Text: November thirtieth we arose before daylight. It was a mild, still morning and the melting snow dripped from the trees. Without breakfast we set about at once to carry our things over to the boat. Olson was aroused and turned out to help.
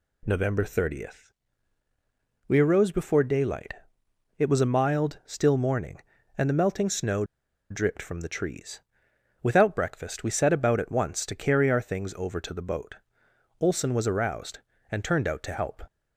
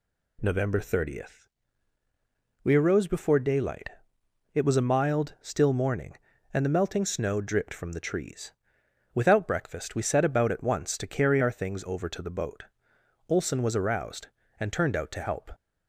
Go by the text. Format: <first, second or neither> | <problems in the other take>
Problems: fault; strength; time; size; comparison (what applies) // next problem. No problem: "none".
second | pauses between "thirtieth" and "we"; at 1.3 s; 1.1 s long; also in the second // pauses between "snow" and "dripped"; noticeable; at 7.2 s; 0.46 s long